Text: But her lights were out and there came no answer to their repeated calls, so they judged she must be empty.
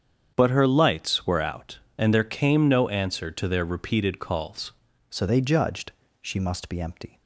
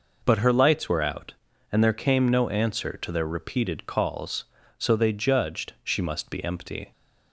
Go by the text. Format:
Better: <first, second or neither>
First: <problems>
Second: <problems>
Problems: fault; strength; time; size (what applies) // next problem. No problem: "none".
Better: second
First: starts louder than the rest; strong; until 1.3 s; 8 dB // changes voice at "so"; from 5.0 s on; 2.2 s long // pauses between "judged" and "she"; slight; at 5.9 s; 0.28 s long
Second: none